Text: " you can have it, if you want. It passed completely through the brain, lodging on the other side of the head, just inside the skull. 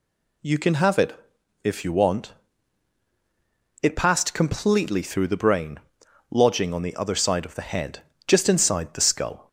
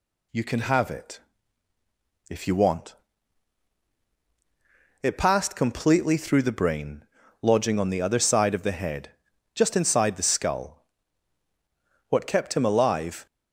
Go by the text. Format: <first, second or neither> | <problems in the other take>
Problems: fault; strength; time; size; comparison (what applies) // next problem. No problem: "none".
first | goes on to say "What kept him alive"; noticeable; from 12.0 s on; 1.1 s long